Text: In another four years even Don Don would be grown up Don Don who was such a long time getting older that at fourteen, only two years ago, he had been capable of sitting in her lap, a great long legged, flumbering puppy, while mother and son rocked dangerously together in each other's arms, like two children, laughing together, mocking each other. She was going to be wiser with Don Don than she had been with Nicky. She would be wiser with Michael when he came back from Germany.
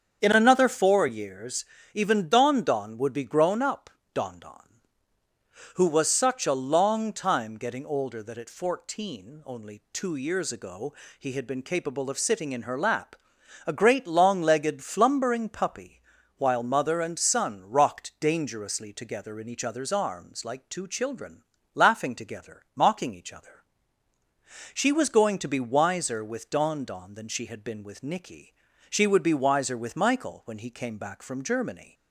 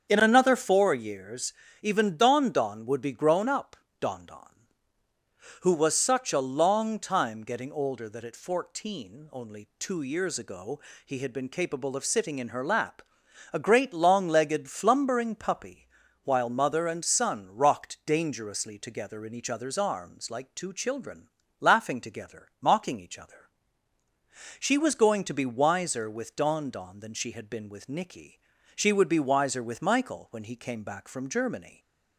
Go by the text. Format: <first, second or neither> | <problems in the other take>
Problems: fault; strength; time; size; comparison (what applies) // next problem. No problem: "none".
neither | starts louder than the rest; strong; the same in both // pauses between "years" and "even"; slight; the same in both // pauses between "up" and "Don"; slight; the same in both